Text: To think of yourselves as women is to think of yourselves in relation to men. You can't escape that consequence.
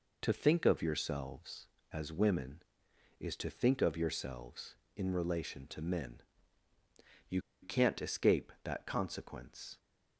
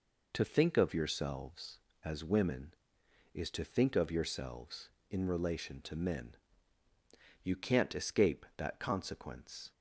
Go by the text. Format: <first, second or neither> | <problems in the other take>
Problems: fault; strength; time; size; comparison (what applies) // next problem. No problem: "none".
second | pauses between "You" and "can't"; slight; at 7.4 s; 0.21 s long